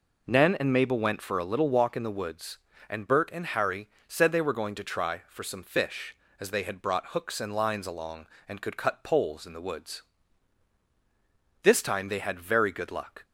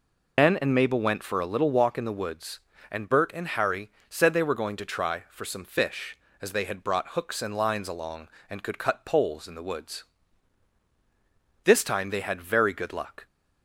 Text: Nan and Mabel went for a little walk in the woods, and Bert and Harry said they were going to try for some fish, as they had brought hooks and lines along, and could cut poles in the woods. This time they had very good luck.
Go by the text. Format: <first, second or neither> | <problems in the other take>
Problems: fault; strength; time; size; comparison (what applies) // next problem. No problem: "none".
first | loses the start of "Nan"; at 0.3 s; 100 ms // pauses between "Harry" and "said"; slight; at 3.8 s; 0.20 s long; slight in the first